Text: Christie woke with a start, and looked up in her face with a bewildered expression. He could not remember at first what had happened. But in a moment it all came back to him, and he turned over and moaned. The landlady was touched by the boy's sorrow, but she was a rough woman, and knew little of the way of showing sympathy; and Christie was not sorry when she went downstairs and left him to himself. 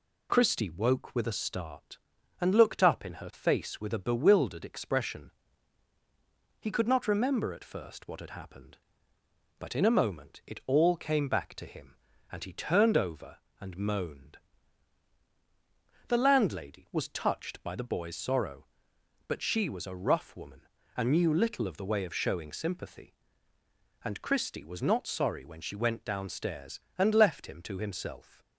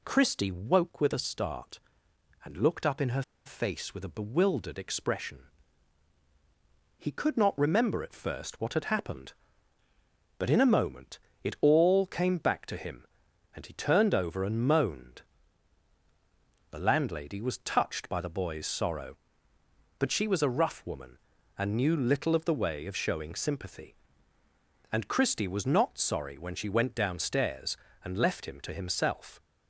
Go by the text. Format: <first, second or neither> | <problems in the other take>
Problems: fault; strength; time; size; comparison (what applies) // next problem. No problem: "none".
first | pauses between "her" and "face"; slight; at 3.2 s; 0.24 s long // pauses between "moment" and "it"; slight; at 11.1 s; 0.24 s long